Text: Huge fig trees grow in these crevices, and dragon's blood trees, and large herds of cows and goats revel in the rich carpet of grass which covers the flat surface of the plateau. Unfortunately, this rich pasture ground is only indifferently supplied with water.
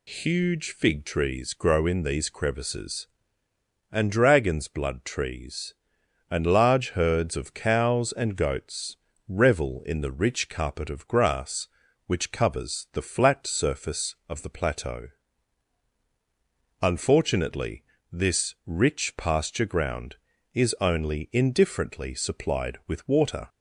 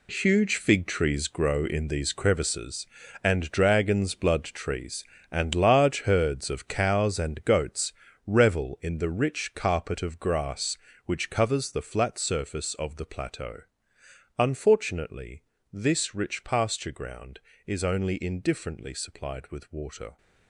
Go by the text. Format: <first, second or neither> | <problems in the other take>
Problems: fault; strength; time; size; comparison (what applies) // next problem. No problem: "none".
first | gets quieter; strong; throughout; 11 dB // pauses between "goats" and "revel"; slight; at 7.9 s; 0.34 s long; slight in the first